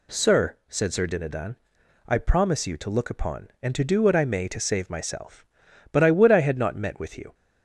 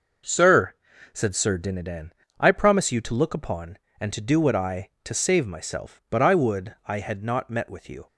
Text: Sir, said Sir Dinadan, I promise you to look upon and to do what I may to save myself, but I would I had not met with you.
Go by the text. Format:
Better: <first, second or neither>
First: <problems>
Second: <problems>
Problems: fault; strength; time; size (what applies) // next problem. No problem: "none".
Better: first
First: none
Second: skips "may"; at 4.9 s